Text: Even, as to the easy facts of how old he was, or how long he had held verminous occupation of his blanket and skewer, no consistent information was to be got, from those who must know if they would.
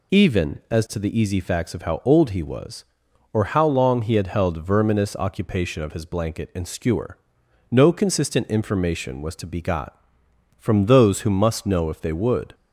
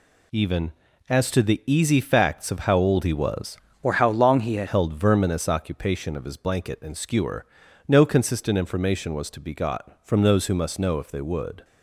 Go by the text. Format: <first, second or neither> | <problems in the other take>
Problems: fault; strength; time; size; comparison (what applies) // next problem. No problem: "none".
first | changes voice from "or" to "had"; from 3.8 to 4.6 s; 0.8 s long